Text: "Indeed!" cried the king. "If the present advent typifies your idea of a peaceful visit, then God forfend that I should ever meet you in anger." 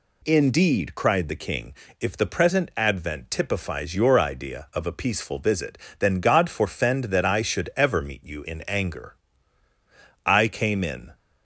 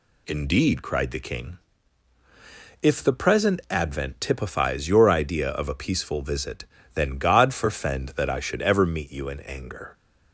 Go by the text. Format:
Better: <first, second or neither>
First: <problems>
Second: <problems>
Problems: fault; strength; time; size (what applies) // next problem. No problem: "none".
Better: second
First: goes on to say "I came in"; noticeable; from 10.2 s on; 0.86 s long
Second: none